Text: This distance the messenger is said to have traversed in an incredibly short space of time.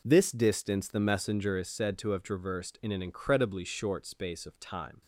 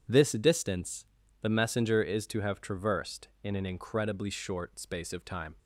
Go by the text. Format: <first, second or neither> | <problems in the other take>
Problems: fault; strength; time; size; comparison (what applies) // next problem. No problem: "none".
first | pauses between "distance" and "the"; at 1.0 s; 0.38 s long // skips "said"; at 2.2 s